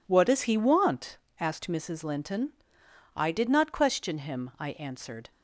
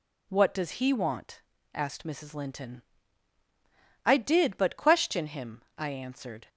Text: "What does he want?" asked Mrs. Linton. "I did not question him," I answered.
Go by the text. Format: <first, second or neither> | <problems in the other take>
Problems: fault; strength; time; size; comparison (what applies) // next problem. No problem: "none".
first | says "but" for "not"; at 4.5 s